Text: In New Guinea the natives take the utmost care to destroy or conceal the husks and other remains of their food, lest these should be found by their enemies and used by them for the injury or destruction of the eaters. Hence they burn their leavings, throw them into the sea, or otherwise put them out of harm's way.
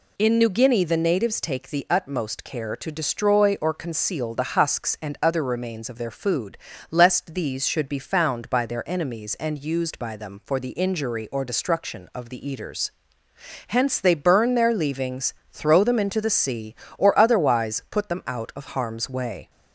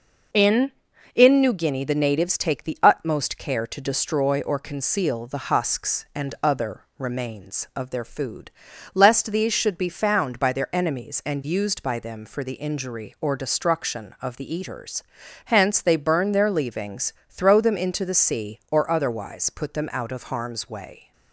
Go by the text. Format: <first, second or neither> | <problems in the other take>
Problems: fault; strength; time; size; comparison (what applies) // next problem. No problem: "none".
first | says "In" twice; at 1.1 s